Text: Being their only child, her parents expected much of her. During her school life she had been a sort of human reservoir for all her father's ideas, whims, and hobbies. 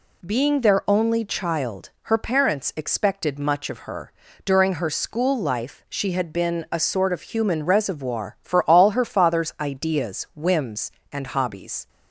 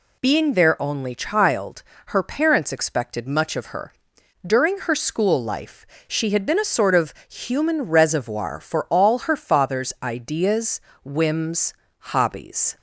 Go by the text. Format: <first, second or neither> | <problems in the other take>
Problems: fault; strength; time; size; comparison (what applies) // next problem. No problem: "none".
first | pauses between "life" and "she"; slight; at 5.8 s; 0.22 s long // pauses between "of" and "human"; slight; at 7.1 s; 0.16 s long // skips "and"; at 11.8 s